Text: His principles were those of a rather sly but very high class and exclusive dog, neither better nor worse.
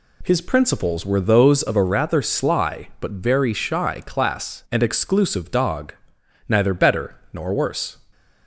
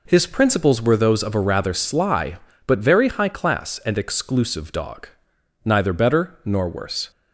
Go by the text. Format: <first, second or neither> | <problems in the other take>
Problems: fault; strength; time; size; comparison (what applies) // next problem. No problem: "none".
second | says "shy" for "high"; at 3.5 s // pauses between "better" and "nor"; slight; at 7.1 s; 0.16 s long